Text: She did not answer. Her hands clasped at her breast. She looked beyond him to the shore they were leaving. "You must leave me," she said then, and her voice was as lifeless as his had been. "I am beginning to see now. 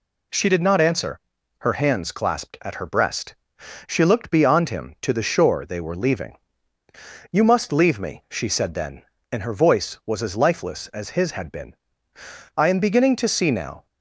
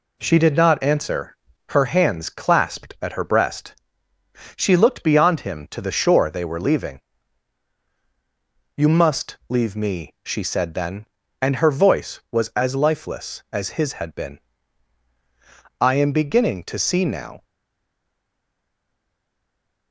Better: first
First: none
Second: stays silent after the last word; from 17.4 s on; 2.5 s long

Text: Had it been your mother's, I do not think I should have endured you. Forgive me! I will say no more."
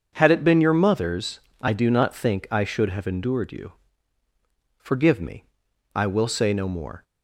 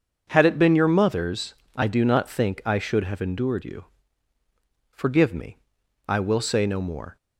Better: neither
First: starts louder than the rest; until 1.1 s; 7 dB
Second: starts louder than the rest; until 1.3 s; 6.5 dB

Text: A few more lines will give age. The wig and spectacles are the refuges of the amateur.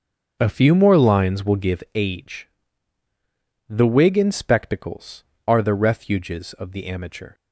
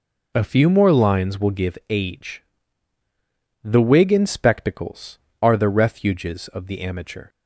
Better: second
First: starts louder than the rest; until 2.2 s; 7 dB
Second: none

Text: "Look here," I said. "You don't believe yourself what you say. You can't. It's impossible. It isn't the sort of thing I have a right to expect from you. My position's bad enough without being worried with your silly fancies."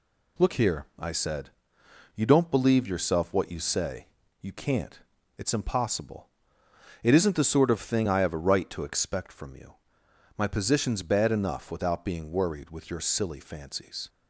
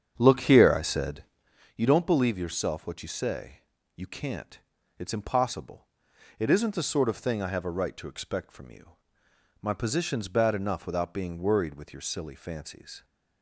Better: first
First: none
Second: starts louder than the rest; strong; until 1.6 s; 8 dB

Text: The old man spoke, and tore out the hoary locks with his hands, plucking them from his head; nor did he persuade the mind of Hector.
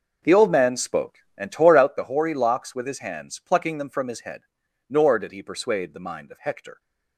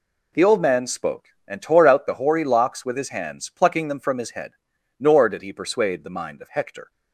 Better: second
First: starts louder than the rest; noticeable; until 1.9 s; 6 dB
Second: none

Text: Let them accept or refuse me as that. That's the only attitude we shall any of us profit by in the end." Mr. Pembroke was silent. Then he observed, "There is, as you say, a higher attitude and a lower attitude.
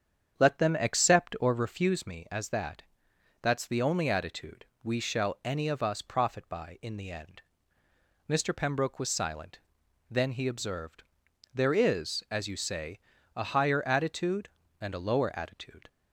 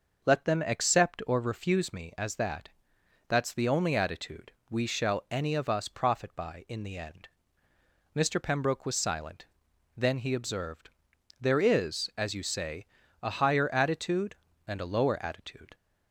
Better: second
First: starts louder than the rest; strong; until 1.9 s; 8 dB // pauses between "attitude" and "we"; slight; at 4.6 s; 0.18 s long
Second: pauses between "attitude" and "we"; slight; at 4.5 s; 0.18 s long

